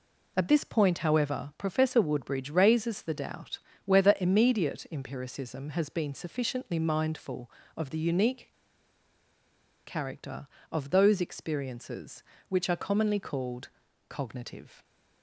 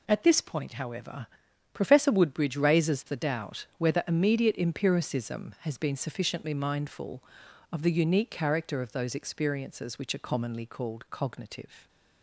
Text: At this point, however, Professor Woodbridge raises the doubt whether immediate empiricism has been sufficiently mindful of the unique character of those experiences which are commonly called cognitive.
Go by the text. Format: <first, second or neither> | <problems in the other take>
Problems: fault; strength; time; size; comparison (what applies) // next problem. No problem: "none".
second | pauses between "doubt" and "whether"; slight; at 3.5 s; 0.26 s long // pauses between "unique" and "character"; strong; at 8.4 s; 1.3 s long // pauses between "called" and "cognitive"; at 13.6 s; 0.40 s long